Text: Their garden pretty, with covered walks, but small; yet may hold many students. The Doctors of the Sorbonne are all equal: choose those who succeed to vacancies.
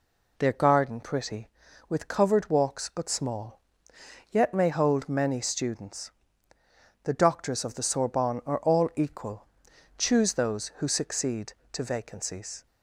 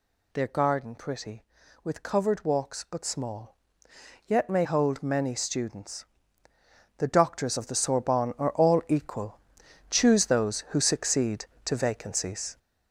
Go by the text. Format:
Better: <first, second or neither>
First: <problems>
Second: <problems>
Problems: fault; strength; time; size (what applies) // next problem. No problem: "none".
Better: first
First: none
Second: gets louder; throughout; 7 dB